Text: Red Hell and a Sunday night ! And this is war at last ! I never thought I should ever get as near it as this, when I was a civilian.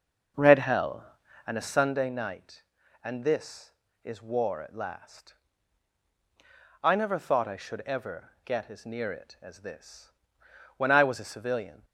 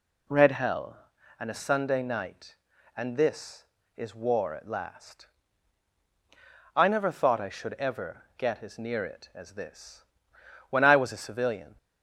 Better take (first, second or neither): second